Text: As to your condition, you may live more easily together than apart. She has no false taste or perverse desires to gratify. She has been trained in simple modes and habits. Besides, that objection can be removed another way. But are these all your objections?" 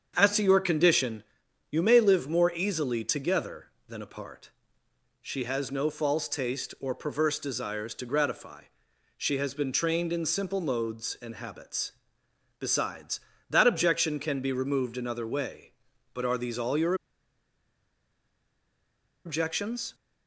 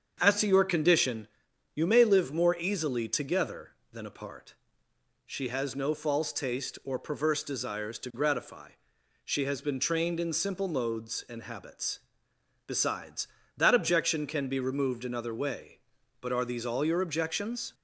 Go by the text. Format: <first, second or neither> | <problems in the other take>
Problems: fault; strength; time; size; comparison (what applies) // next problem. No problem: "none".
second | starts louder than the rest; strong; until 1.1 s; 7.5 dB; strong in the second // pauses between "your" and "objections"; strong; at 16.9 s; 2.3 s long